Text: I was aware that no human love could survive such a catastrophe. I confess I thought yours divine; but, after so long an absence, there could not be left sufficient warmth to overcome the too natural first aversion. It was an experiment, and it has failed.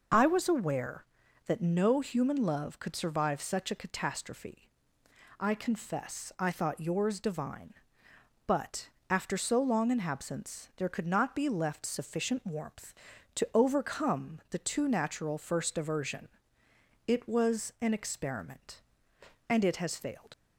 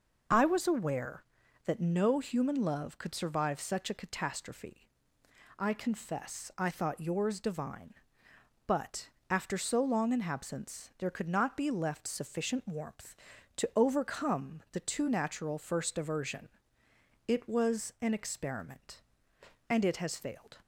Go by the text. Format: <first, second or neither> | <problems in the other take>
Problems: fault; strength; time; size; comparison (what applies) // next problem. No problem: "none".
second | leaves "failed" unfinished; at 20.3 s; 70 ms